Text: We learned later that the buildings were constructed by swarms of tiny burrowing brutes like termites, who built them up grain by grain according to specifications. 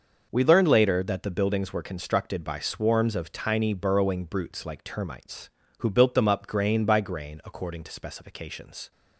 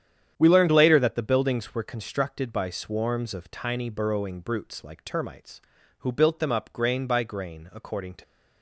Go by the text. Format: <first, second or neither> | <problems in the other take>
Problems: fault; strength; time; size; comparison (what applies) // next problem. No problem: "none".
first | starts louder than the rest; strong; until 1.3 s; 9.5 dB // stops before "specifications"; at 8.2 s